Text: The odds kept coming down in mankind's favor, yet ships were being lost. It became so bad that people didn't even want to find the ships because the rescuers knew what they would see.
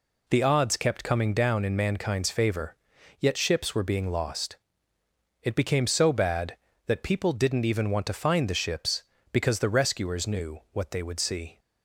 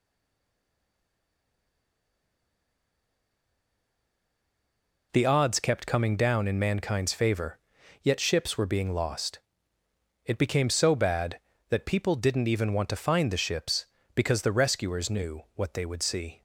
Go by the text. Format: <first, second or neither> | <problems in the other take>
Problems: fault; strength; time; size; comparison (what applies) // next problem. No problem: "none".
first | stays silent before the first word; strong; until 5.1 s; 5.1 s long